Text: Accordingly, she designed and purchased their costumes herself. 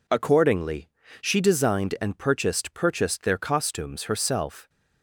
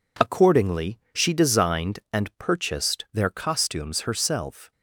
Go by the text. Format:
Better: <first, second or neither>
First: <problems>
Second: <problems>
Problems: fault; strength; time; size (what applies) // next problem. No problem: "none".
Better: second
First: says "purchased" twice; at 2.7 s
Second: none